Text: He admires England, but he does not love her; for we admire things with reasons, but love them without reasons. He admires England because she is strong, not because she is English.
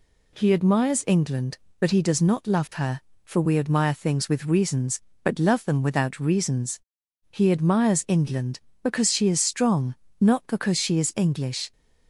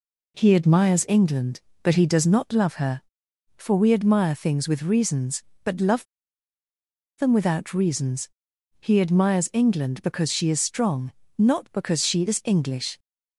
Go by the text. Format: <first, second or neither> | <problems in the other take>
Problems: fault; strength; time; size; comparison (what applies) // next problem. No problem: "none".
first | pauses between "love" and "them"; at 6.0 s; 1.1 s long